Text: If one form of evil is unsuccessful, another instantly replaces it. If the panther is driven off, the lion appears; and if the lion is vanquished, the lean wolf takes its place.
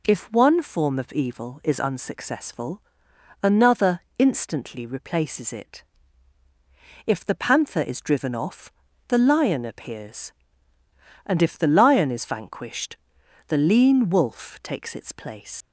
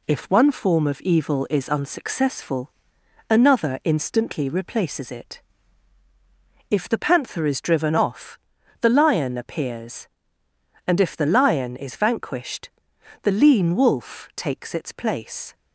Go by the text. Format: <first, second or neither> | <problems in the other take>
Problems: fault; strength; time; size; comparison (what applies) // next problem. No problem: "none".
second | pauses between "another" and "instantly"; slight; at 4.0 s; 0.18 s long // leaves "place" unfinished; at 15.6 s; 105 ms